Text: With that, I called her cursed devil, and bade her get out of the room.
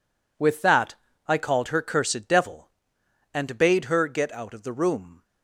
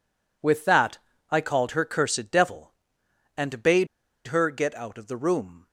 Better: first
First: none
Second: pauses between "bade" and "her"; at 3.8 s; 0.41 s long

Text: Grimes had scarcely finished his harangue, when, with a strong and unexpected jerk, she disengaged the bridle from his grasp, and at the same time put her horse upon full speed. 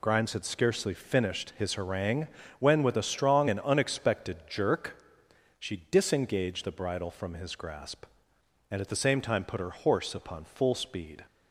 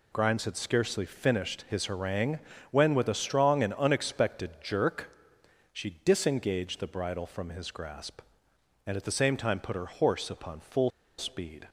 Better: first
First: none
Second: pauses between "full" and "speed"; slight; at 10.9 s; 0.28 s long

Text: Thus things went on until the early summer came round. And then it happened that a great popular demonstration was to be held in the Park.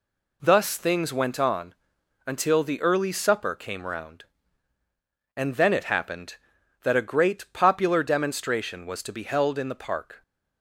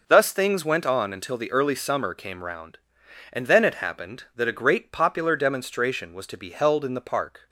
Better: second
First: pauses between "on" and "until"; noticeable; at 1.7 s; 0.52 s long // says "supper" for "summer"; at 3.1 s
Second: none

